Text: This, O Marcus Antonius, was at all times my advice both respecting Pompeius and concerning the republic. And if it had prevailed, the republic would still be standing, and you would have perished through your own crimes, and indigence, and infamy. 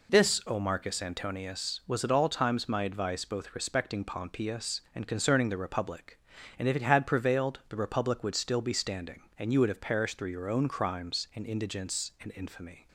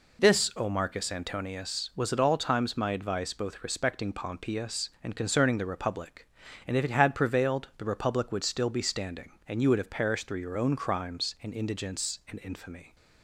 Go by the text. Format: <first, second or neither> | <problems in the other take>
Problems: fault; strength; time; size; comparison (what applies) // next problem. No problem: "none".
neither | none